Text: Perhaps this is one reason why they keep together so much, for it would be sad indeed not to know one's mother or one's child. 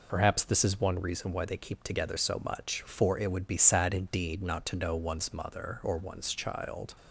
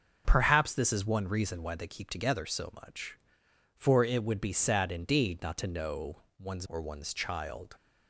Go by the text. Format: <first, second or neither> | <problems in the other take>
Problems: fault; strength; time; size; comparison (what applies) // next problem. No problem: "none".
first | starts louder than the rest; until 1.2 s; 6.5 dB // pauses between "know" and "one's"; slight; at 6.1 s; 0.20 s long // skips "mother"; at 6.6 s